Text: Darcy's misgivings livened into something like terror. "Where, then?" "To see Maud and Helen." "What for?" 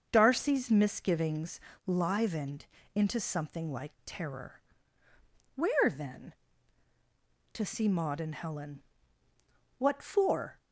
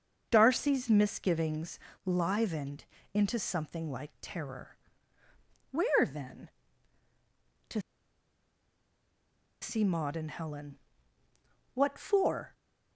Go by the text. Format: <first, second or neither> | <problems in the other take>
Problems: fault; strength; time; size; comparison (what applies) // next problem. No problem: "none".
first | starts louder than the rest; until 1.3 s; 6 dB; also in the first // pauses between "misgivings" and "livened"; slight; at 1.7 s; 0.24 s long; slight in the first // pauses between "livened" and "into"; slight; at 2.8 s; 0.30 s long; slight in the first // pauses between "To" and "see"; strong; at 7.7 s; 1.8 s long